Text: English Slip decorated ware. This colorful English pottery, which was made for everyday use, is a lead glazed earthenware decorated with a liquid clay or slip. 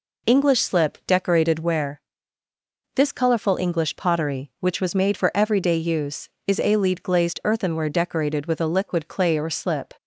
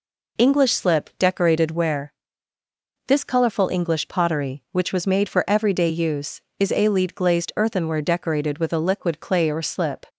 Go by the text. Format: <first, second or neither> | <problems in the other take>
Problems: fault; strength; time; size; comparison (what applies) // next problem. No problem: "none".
neither | none